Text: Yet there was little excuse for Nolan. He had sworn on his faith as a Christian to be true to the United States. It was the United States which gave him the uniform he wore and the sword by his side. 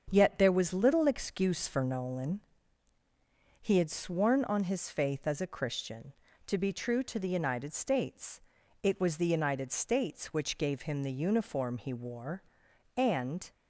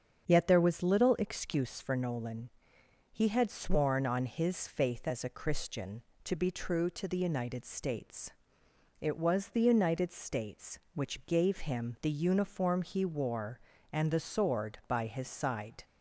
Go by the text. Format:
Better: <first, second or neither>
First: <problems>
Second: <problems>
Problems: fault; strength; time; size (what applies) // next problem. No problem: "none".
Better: second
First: starts louder than the rest; strong; until 1.1 s; 7.5 dB // stops before "the sword by his side"; at 13.5 s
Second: starts louder than the rest; strong; until 1.2 s; 7 dB